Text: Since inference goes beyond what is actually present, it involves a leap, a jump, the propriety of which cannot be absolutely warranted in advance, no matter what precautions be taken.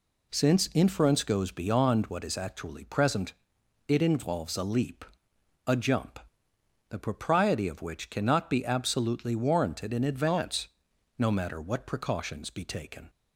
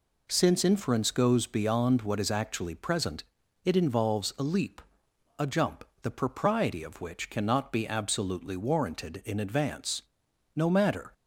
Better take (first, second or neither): first